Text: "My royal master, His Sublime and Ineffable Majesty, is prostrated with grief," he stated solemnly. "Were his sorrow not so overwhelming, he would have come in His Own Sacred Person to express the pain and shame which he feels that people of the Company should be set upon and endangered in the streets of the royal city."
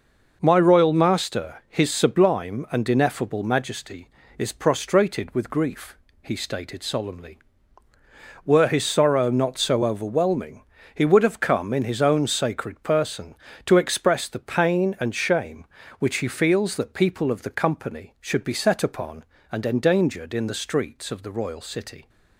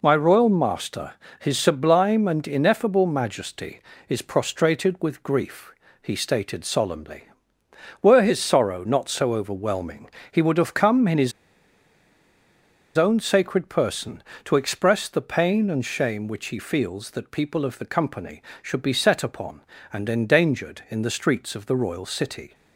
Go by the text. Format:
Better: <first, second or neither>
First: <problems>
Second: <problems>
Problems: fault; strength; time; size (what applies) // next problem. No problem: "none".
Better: first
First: none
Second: pauses between "His" and "Own"; strong; at 11.3 s; 1.6 s long